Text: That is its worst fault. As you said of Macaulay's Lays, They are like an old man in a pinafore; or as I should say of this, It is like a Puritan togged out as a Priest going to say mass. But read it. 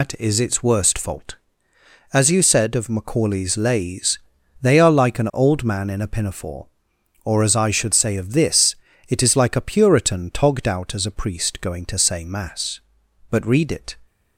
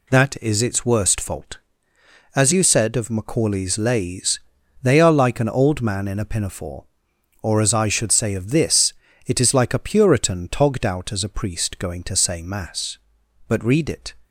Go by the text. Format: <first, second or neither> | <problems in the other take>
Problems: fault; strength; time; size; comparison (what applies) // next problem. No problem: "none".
second | loses the start of "That"; at 0.0 s; 130 ms